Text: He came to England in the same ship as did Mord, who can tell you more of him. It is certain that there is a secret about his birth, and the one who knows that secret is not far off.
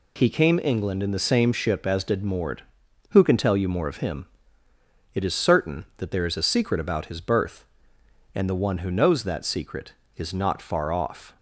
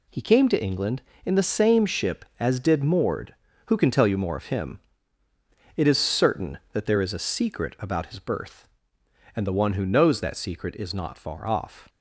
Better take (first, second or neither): second